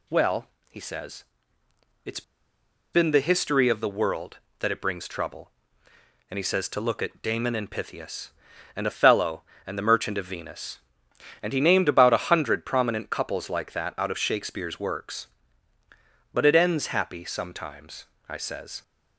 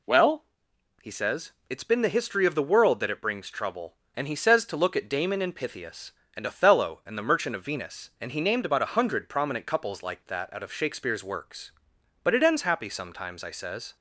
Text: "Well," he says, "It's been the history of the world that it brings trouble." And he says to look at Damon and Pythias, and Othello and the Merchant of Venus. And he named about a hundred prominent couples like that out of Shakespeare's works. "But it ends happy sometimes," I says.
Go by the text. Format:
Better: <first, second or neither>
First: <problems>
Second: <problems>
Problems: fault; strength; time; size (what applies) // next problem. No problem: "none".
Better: second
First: pauses between "It's" and "been"; noticeable; at 2.2 s; 0.71 s long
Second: none